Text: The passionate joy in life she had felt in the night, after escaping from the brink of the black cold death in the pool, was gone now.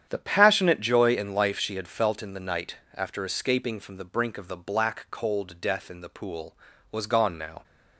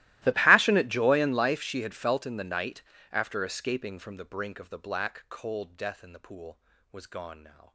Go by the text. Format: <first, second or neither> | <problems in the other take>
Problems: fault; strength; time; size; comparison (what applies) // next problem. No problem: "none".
first | gets quieter; strong; throughout; 27 dB // starts louder than the rest; strong; until 1.2 s; 16.5 dB; strong in the first